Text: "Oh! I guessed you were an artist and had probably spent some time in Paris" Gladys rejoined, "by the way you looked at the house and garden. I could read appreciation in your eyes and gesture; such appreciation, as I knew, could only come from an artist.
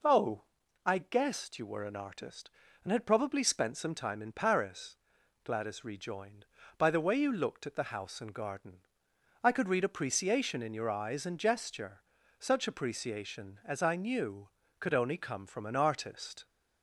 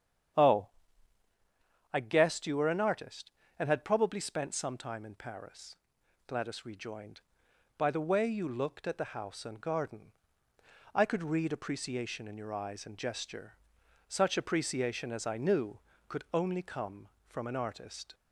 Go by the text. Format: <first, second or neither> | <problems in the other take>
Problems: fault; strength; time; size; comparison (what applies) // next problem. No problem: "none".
first | starts louder than the rest; strong; until 1.4 s; 8.5 dB // pauses between "Paris" and "Gladys"; noticeable; at 5.7 s; 0.52 s long; noticeable in the first